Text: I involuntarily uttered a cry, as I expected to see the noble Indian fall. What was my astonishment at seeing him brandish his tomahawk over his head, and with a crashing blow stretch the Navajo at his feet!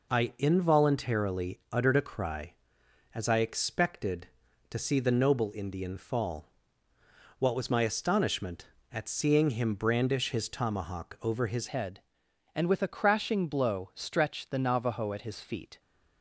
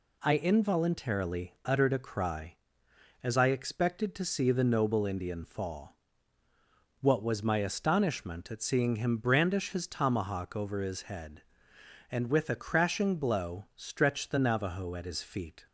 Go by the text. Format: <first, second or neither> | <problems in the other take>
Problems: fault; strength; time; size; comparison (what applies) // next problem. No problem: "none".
second | changes voice at "head"; from 11.6 s on; 4.1 s long